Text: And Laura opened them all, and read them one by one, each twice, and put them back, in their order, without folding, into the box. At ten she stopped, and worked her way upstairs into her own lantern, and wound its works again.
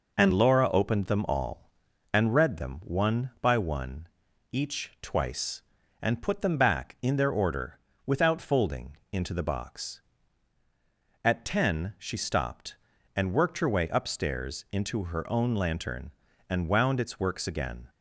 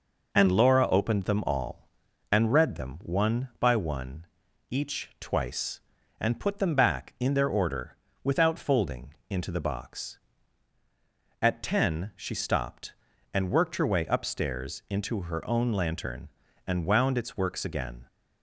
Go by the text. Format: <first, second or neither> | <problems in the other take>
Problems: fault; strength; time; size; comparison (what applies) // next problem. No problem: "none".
neither | none